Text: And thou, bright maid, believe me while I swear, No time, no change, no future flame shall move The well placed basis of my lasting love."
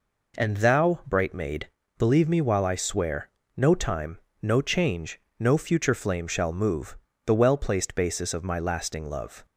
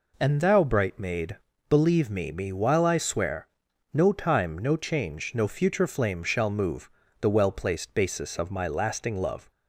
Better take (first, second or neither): first